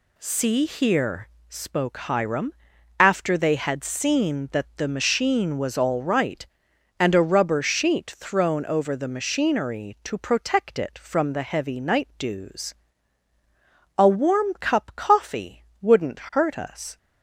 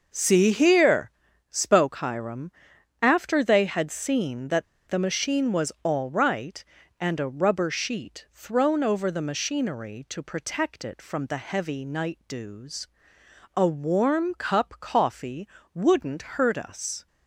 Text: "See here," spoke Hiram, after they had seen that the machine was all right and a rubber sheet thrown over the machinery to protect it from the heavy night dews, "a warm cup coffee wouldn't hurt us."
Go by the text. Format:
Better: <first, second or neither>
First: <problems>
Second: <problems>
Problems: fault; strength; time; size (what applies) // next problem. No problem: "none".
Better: first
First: pauses between "coffee" and "wouldn't"; slight; at 15.6 s; 0.16 s long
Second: pauses between "that" and "the"; slight; at 4.6 s; 0.24 s long // pauses between "coffee" and "wouldn't"; slight; at 15.4 s; 0.24 s long